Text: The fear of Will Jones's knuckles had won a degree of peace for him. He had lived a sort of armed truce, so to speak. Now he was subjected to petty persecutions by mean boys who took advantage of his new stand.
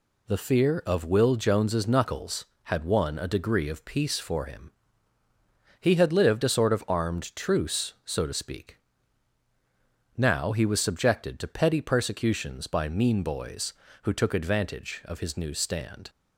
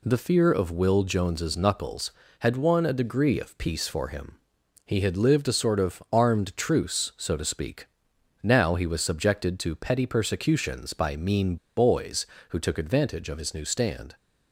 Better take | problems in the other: first | pauses between "mean" and "boys"; slight; at 11.5 s; 0.21 s long

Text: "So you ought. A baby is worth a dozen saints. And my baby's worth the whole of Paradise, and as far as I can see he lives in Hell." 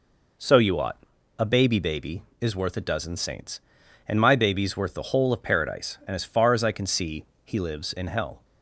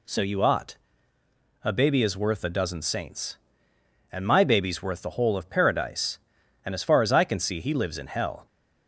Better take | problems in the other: second | says "baby" twice; at 1.7 s // pauses between "see" and "he"; slight; at 7.2 s; 0.20 s long

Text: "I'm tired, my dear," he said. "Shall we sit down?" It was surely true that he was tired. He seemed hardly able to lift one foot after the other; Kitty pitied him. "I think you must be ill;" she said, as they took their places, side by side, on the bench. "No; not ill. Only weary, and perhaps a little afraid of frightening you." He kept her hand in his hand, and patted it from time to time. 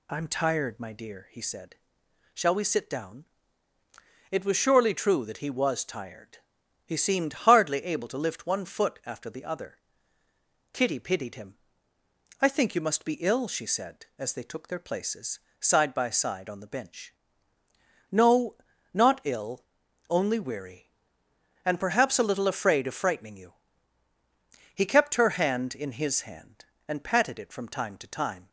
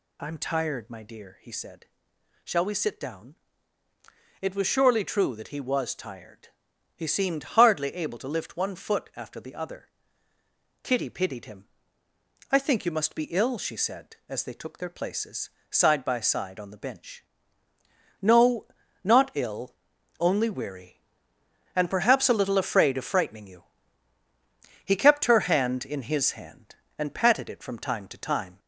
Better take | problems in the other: first | gets louder; throughout; 3.5 dB

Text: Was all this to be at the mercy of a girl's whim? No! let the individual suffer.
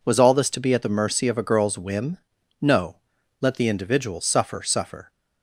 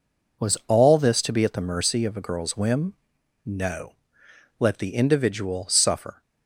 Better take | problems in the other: second | says "suffer" twice; at 4.6 s

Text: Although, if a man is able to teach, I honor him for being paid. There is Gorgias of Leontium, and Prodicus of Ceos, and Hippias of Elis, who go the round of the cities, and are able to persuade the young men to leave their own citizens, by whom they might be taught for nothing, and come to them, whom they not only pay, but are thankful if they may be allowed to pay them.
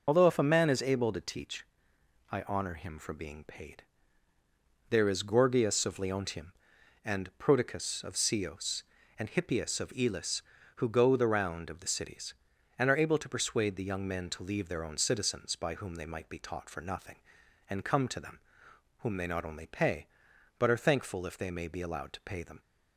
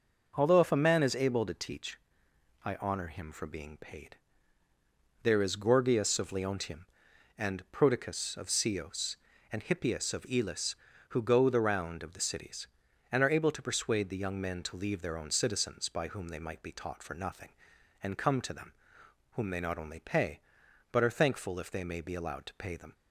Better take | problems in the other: second | loses the start of "Although"; at 0.0 s; 80 ms

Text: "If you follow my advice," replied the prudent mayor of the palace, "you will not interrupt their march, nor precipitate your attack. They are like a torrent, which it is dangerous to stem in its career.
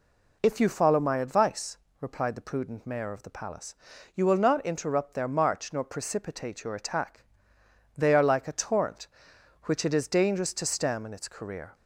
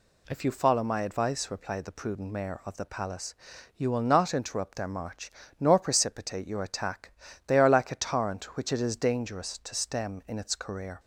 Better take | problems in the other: neither | none

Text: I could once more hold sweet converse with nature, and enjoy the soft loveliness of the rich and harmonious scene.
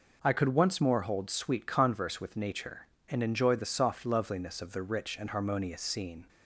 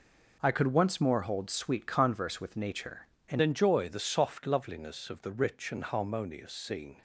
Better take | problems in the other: first | changes voice at "enjoy"; from 3.3 s on; 3.7 s long

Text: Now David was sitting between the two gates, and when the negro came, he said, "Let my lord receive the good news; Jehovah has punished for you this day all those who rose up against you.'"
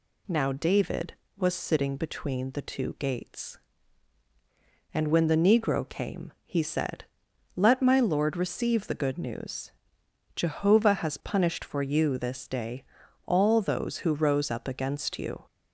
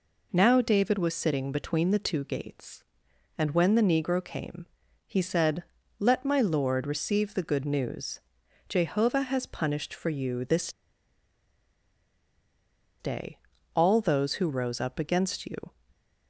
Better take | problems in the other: first | pauses between "this" and "day"; strong; at 10.7 s; 2.2 s long // pauses between "day" and "all"; slight; at 13.3 s; 0.36 s long; also in the first

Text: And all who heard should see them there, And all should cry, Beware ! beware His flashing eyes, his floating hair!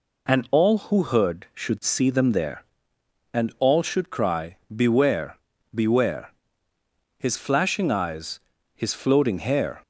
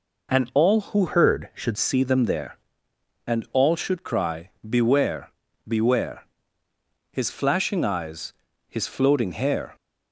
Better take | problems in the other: first | changes voice from "heard" to "should"; from 1.0 to 1.7 s; 0.7 s long // pauses between "beware" and "His"; noticeable; at 6.2 s; 0.88 s long; noticeable in the first

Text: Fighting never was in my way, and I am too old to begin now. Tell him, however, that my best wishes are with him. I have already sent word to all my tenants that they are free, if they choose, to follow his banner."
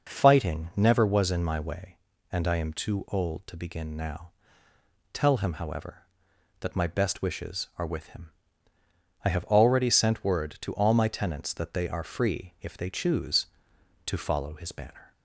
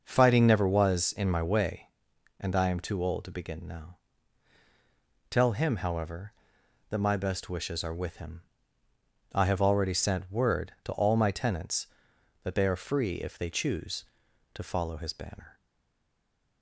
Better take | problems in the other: first | stays silent after the last word; from 15.5 s on; 1.1 s long

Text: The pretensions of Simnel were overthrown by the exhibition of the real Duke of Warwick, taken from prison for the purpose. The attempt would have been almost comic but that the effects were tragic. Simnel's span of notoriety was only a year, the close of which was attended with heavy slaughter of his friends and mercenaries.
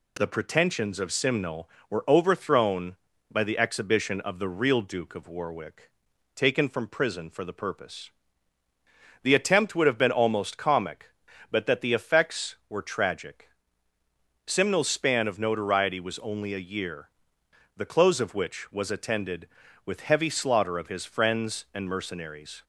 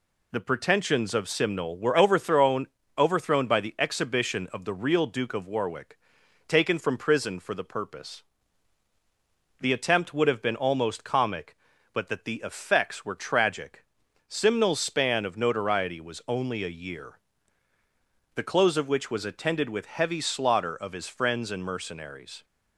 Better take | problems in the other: first | says "overthrown" twice; at 2.9 s

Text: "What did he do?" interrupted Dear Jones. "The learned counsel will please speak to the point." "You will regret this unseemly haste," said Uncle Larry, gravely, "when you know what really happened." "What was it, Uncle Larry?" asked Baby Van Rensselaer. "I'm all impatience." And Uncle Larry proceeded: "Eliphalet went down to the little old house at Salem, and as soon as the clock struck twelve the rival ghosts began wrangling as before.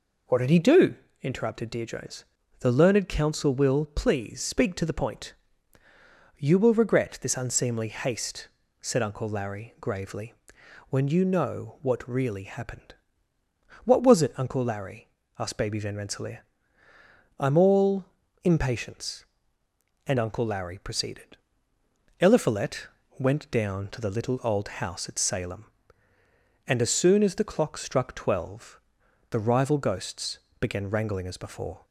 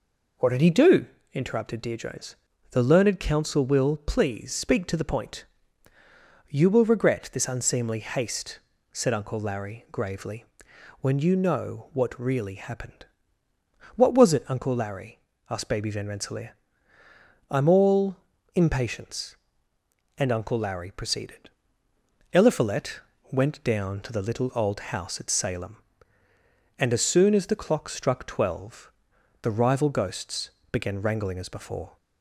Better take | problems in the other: neither | pauses between "all" and "impatience"; the same in both // pauses between "Eliphalet" and "went"; slight; the same in both // pauses between "twelve" and "the"; noticeable; the same in both // pauses between "ghosts" and "began"; slight; the same in both

